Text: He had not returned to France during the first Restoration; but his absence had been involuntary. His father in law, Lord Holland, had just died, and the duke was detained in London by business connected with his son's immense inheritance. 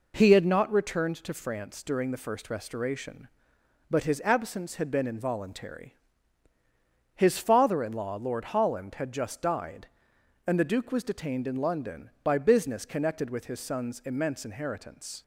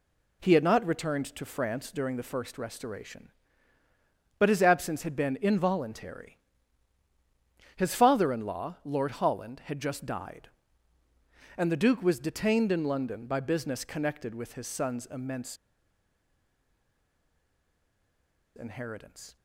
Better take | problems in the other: first | pauses between "immense" and "inheritance"; strong; at 15.5 s; 2.9 s long

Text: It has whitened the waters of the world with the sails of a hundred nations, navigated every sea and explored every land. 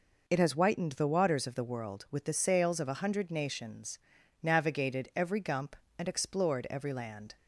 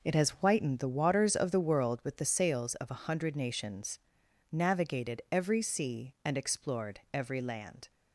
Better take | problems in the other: second | says "gump" for "sea"; at 5.3 s

